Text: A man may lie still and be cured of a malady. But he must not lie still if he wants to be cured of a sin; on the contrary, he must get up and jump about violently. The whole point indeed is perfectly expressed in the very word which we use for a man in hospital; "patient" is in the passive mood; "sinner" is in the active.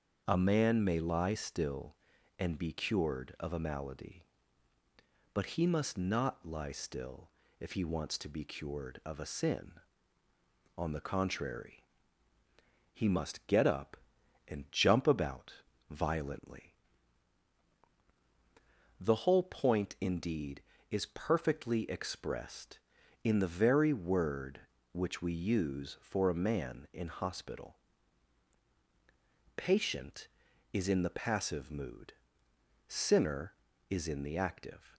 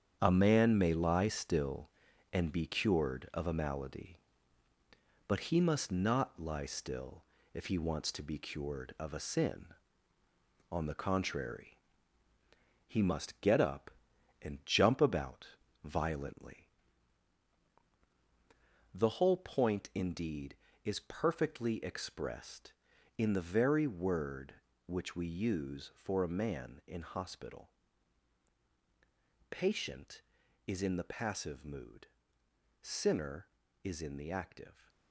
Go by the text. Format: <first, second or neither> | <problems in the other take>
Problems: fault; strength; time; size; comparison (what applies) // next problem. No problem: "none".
first | gets quieter; strong; throughout; 8.5 dB // starts louder than the rest; strong; until 1.2 s; 8 dB; also in the first // pauses between "still" and "if"; slight; at 7.2 s; 0.30 s long; slight in the first // pauses between "about" and "violently"; at 15.4 s; 0.38 s long; also in the first